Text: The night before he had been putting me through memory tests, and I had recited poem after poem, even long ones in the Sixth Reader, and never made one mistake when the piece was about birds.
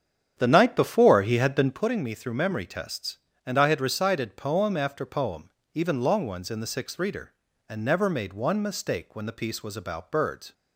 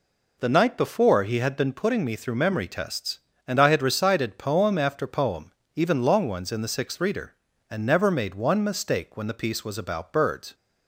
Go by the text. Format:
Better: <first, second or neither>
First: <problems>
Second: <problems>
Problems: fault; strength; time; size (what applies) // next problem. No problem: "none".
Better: second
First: starts louder than the rest; strong; until 1.9 s; 8.5 dB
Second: none